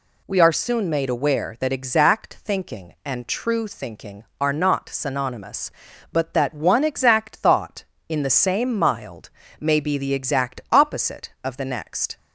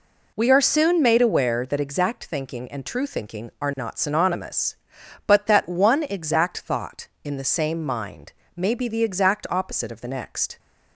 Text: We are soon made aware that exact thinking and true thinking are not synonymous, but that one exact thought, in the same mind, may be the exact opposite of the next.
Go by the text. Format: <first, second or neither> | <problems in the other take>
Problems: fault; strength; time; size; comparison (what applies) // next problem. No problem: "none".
second | says "mild" for "mind"; at 8.7 s